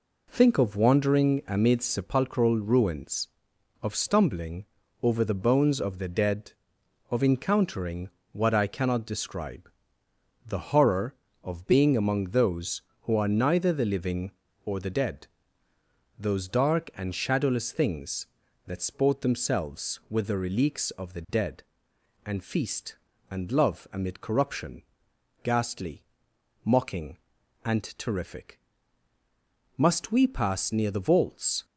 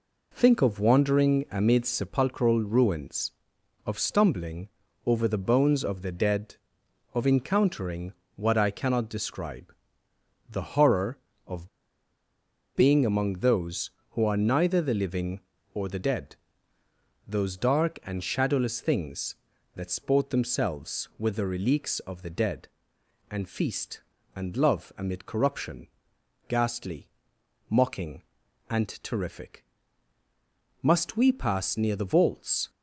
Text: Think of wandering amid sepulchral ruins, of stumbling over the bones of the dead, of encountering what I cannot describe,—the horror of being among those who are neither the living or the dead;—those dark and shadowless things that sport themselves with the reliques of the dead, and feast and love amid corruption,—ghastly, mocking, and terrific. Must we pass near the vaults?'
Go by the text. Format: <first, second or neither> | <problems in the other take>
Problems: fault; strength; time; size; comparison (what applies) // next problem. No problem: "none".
first | pauses between "stumbling" and "over"; at 4.6 s; 0.38 s long; also in the first // pauses between "encountering" and "what"; slight; at 8.1 s; 0.22 s long; slight in the first // pauses between "of" and "being"; at 11.6 s; 1.0 s long